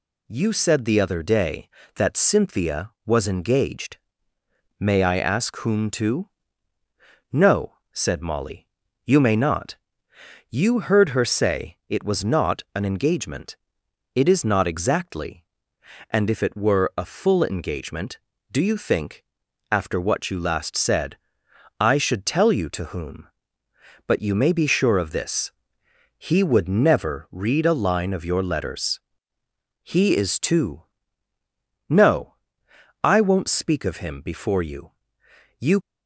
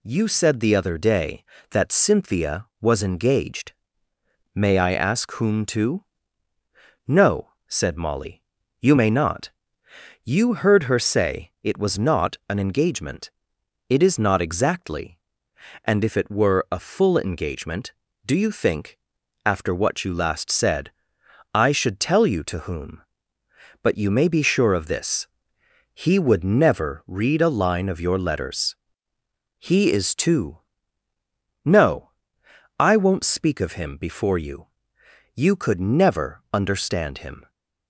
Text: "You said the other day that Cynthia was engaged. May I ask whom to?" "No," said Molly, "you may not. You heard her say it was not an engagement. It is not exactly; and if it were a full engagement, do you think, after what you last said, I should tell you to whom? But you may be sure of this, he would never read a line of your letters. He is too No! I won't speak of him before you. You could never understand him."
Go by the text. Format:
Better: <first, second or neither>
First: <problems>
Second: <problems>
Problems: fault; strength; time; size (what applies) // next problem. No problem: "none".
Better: second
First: pauses between "too" and "No"; at 30.8 s; 1.0 s long // stops before "could never understand him"; at 35.8 s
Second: pauses between "too" and "No"; at 30.5 s; 1.0 s long